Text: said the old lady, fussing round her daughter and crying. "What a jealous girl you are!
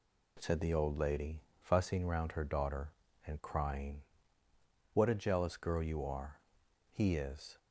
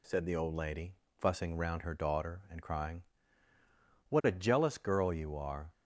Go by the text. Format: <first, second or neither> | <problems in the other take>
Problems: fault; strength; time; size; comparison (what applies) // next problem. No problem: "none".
second | goes on to say "He is"; noticeable; from 6.9 s on; 0.64 s long